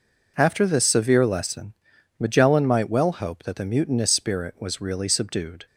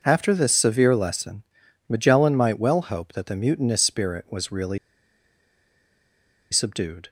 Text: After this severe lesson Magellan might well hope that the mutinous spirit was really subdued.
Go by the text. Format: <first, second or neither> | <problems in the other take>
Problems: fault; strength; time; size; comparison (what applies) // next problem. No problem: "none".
first | pauses between "lesson" and "Magellan"; at 1.4 s; 0.44 s long; also in the first // pauses between "really" and "subdued"; strong; at 4.7 s; 1.7 s long